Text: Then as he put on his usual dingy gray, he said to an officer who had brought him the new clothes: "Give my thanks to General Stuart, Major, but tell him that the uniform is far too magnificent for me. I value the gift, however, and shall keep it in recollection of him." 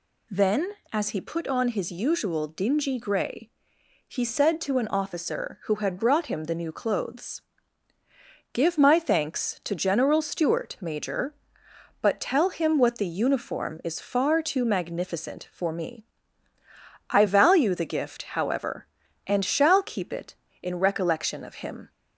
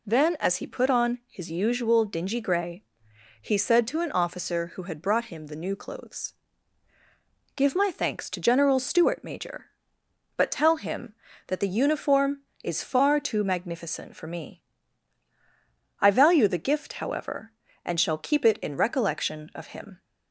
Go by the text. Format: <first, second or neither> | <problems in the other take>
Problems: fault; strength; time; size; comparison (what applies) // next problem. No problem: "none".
second | says "what" for "that"; at 12.7 s